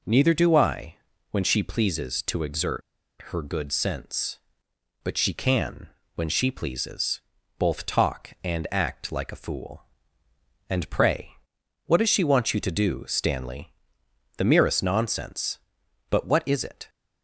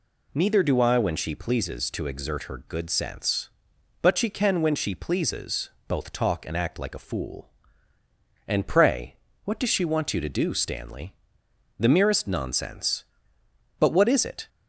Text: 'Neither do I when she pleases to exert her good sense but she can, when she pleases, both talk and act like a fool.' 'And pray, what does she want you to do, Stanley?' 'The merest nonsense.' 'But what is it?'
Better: second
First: pauses between "I" and "when"; slight; at 0.9 s; 0.34 s long // pauses between "exert" and "her"; at 2.8 s; 0.45 s long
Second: none

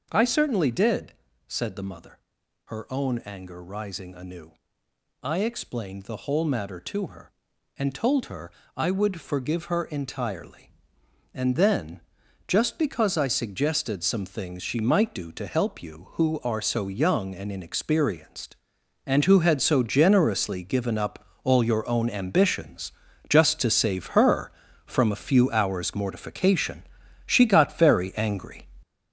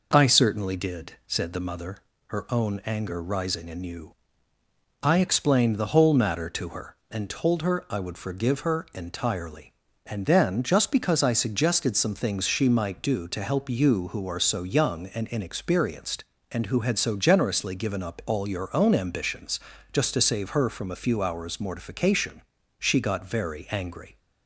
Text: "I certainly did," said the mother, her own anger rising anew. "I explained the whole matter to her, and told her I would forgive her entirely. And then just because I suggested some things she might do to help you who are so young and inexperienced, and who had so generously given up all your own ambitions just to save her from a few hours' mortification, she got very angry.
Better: second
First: gets louder; throughout; 6.5 dB // pauses between "her" and "I"; slight; at 8.5 s; 0.24 s long // pauses between "then" and "just"; noticeable; at 12.0 s; 0.46 s long // pauses between "up" and "all"; slight; at 21.2 s; 0.20 s long // pauses between "ambitions" and "just"; at 22.9 s; 0.38 s long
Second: pauses between "ambitions" and "just"; slight; at 19.5 s; 0.34 s long

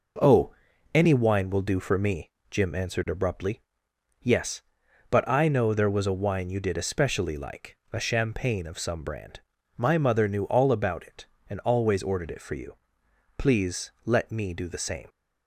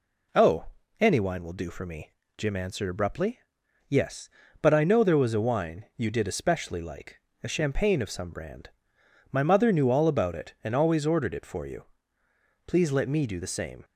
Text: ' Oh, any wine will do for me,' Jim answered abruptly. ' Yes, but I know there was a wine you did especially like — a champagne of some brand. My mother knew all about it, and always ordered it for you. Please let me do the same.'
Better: neither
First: none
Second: none

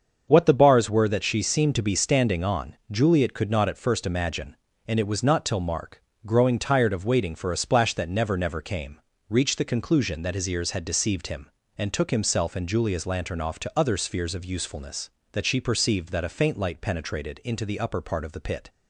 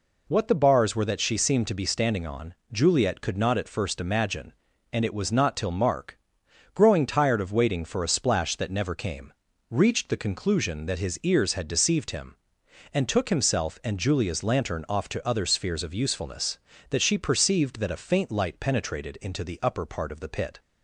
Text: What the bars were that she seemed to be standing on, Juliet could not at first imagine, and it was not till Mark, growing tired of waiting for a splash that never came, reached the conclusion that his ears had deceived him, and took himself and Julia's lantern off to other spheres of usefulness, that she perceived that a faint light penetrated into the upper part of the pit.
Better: second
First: starts louder than the rest; until 1.2 s; 7 dB // says "never" twice; at 8.3 s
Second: none

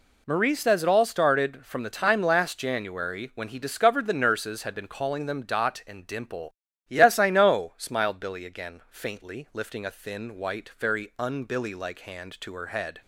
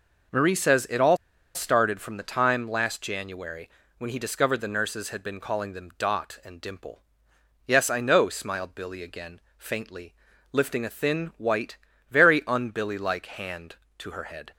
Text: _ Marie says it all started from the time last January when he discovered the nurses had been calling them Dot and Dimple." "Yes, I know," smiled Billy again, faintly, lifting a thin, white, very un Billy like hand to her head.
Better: first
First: none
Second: pauses between "all" and "started"; at 1.1 s; 0.38 s long // pauses between "January" and "when"; slight; at 3.6 s; 0.30 s long

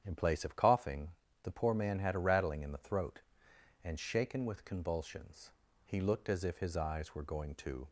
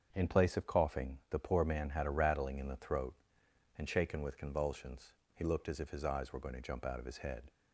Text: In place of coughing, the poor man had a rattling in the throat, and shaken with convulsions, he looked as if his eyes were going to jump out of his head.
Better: second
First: starts louder than the rest; strong; until 1.0 s; 9 dB // stops before "jump out of his head"; at 7.8 s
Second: starts louder than the rest; until 1.1 s; 7 dB

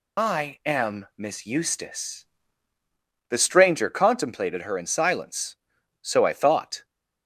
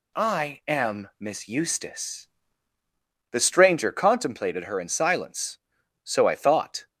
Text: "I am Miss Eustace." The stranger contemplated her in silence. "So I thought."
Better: second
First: loses the start of "I"; at 0.1 s; 40 ms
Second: none

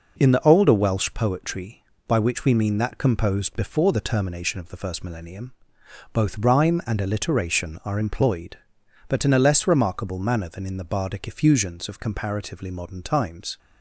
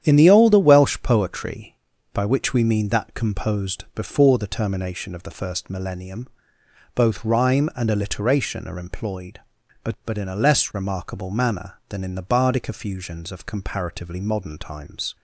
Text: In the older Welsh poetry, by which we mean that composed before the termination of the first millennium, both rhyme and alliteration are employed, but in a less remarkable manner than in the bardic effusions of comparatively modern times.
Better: first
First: none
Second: starts louder than the rest; strong; until 1.1 s; 9.5 dB // says "but" twice; at 10.0 s

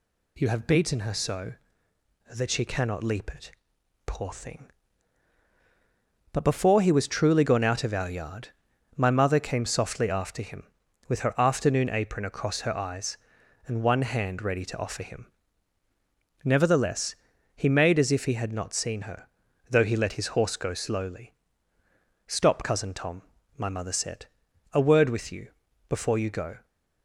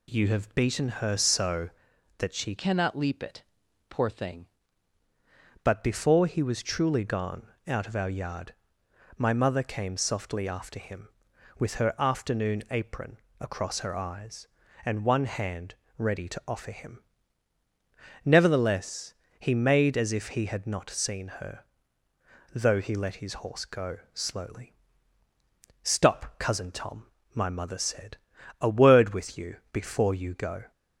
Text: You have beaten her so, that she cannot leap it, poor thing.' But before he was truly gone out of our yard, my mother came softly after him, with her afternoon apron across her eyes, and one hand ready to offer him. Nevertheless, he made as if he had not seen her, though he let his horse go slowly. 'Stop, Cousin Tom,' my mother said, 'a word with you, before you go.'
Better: first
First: none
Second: changes voice from "cannot" to "thing"; from 2.5 to 4.4 s; 1.9 s long // pauses between "gone" and "out"; slight; at 7.4 s; 0.20 s long // pauses between "apron" and "across"; slight; at 13.1 s; 0.24 s long // pauses between "hand" and "ready"; slight; at 15.7 s; 0.22 s long // pauses between "go" and "slowly"; slight; at 23.9 s; 0.16 s long

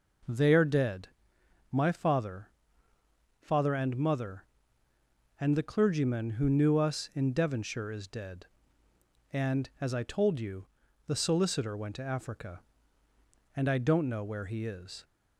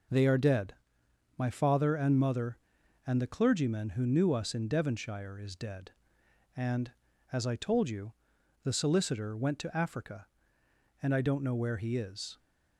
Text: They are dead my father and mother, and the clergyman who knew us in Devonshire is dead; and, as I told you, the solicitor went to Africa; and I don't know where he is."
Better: second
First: pauses between "dead" and "my"; noticeable; at 1.0 s; 0.62 s long // says "father" twice; at 3.4 s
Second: pauses between "dead" and "my"; noticeable; at 0.7 s; 0.64 s long

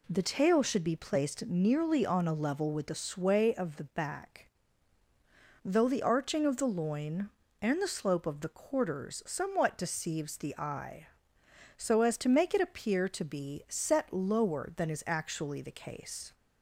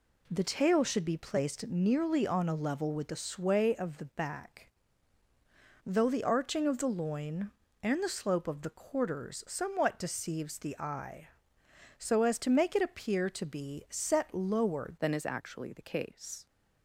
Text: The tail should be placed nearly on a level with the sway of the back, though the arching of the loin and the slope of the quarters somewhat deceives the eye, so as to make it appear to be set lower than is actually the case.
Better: first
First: none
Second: changes voice at "than"; from 14.9 s on; 1.5 s long

